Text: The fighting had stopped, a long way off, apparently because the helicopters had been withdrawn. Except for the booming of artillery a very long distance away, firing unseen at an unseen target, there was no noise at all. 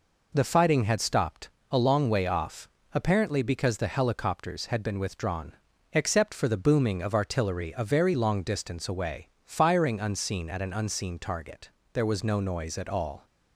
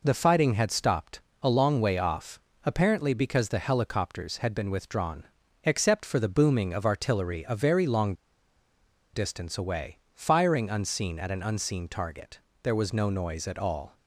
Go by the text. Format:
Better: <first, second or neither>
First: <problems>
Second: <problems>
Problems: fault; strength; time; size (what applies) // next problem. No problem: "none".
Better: first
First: none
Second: pauses between "long" and "distance"; at 8.1 s; 1.0 s long